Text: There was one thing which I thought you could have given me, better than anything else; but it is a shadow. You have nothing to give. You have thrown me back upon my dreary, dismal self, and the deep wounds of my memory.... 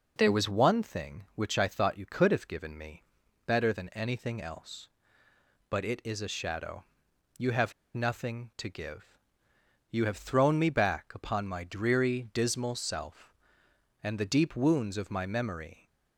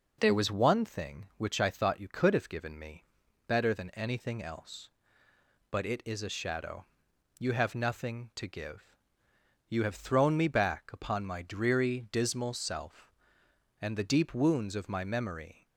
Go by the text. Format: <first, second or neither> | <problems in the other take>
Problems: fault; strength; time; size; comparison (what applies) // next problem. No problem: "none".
second | pauses between "have" and "nothing"; slight; at 7.7 s; 0.23 s long